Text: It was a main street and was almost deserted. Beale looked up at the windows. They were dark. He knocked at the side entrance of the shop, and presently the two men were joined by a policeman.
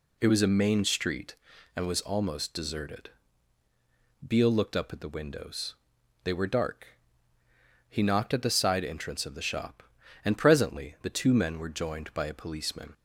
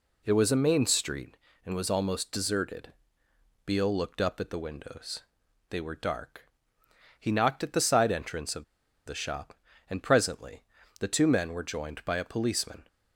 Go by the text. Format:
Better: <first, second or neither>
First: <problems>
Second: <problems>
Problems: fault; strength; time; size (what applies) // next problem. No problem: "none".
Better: first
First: none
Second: pauses between "of" and "the"; at 8.6 s; 0.41 s long // pauses between "presently" and "the"; at 10.6 s; 0.38 s long